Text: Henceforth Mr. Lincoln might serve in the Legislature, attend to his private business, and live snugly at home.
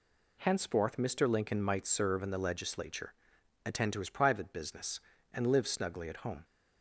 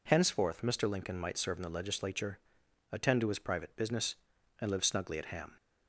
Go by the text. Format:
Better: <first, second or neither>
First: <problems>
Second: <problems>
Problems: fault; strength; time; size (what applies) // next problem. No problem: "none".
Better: first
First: none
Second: says "ham" for "home"; at 5.2 s